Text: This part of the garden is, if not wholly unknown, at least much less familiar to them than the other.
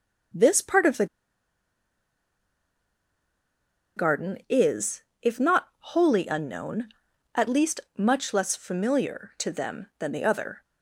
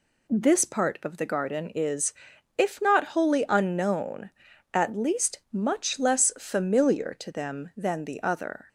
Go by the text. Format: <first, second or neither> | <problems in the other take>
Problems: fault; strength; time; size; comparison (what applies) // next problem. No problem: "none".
second | pauses between "the" and "garden"; strong; at 1.0 s; 2.9 s long // pauses between "least" and "much"; slight; at 7.8 s; 0.16 s long